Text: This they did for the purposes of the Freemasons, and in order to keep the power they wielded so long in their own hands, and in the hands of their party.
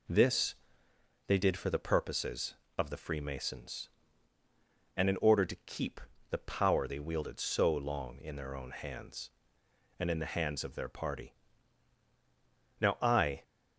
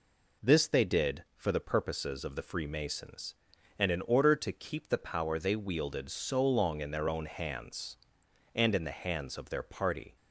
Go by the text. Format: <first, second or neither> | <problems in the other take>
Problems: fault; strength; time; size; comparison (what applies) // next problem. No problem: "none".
second | pauses between "This" and "they"; noticeable; at 0.5 s; 0.74 s long // pauses between "keep" and "the"; slight; at 5.9 s; 0.30 s long // goes on to say "Now I"; noticeable; from 12.8 s on; 0.62 s long